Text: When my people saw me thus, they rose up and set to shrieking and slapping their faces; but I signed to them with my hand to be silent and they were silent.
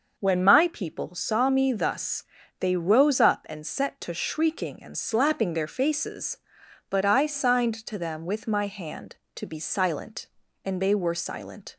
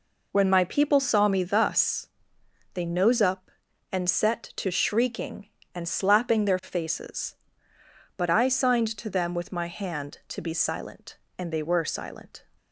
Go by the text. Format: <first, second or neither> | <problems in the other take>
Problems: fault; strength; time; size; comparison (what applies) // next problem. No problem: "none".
first | says "nose" for "rose"; at 2.8 s